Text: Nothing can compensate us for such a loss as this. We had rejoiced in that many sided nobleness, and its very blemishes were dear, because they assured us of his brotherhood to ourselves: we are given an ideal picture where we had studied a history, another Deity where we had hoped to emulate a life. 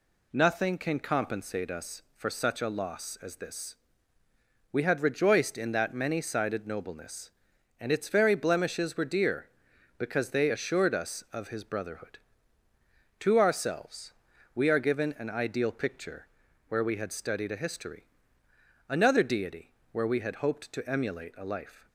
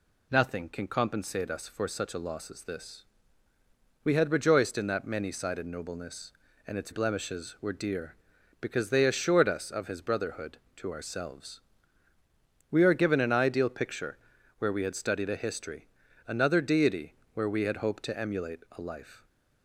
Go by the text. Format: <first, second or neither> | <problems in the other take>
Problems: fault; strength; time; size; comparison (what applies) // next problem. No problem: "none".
first | skips "very"; at 6.9 s // pauses between "picture" and "where"; at 14.1 s; 0.42 s long; also in the first // pauses between "Deity" and "where"; slight; at 17.1 s; 0.20 s long; slight in the first